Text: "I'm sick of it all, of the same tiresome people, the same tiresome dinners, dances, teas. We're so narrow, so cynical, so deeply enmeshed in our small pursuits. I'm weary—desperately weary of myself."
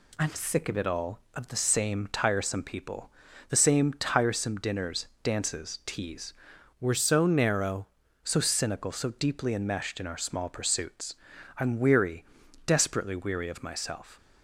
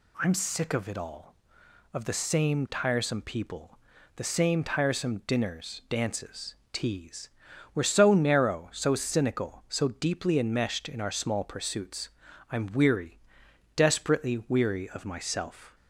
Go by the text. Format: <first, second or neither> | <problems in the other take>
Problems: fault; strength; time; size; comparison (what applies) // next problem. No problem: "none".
second | changes voice from "We're" to "narrow"; from 6.7 to 7.8 s; 1.1 s long